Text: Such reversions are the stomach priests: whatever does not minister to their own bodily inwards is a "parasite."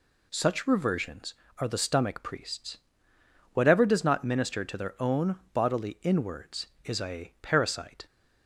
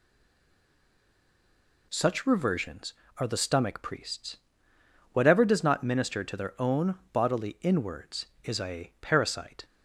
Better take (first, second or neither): first